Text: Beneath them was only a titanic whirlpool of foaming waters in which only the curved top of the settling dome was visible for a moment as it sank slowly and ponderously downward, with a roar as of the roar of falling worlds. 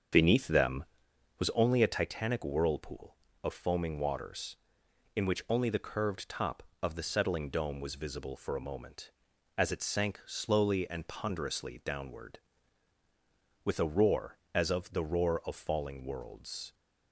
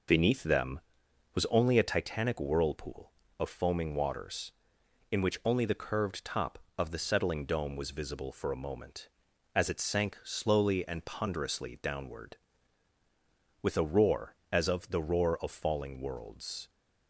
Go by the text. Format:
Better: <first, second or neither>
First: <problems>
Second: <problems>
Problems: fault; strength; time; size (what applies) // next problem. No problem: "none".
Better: second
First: starts louder than the rest; strong; until 1.1 s; 7 dB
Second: none